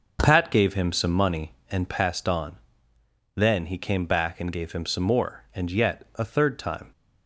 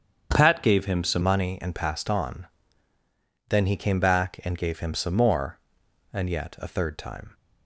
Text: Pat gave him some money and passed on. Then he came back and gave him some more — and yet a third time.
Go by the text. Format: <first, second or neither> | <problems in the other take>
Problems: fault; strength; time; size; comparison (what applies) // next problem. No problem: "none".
first | starts louder than the rest; strong; until 1.3 s; 7.5 dB; noticeable in the first // changes voice at "money"; from 1.2 s on; 6.1 s long